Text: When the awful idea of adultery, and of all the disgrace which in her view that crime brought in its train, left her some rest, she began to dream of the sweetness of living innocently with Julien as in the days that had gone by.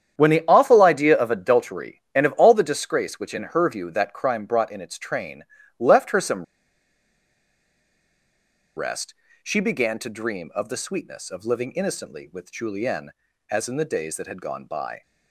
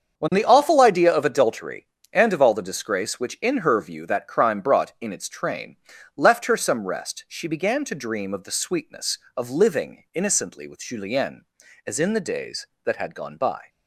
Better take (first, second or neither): second